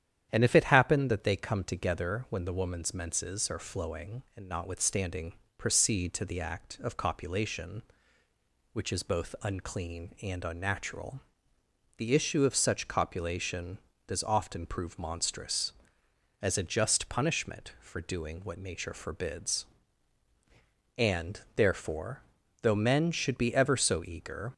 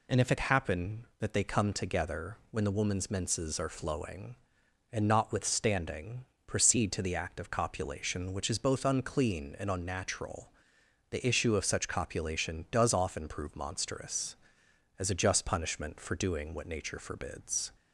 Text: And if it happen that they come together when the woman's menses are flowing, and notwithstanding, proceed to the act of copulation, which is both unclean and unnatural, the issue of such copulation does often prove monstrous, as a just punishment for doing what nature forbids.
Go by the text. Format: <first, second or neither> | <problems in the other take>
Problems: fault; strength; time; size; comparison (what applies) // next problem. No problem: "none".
second | starts louder than the rest; strong; until 1.3 s; 10 dB // goes on to say "And therefore though men should be ever so eager"; strong; from 20.9 s on; 3.5 s long